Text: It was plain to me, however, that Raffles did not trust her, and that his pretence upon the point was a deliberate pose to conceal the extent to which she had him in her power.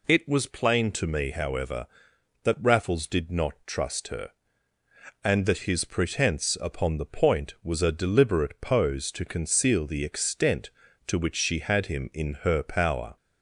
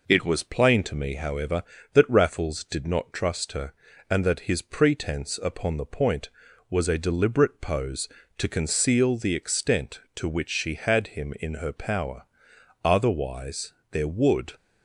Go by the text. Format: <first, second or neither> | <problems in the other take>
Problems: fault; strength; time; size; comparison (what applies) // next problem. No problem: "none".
first | goes on to say "Otherwise there would"; strong; from 12.8 s on; 1.7 s long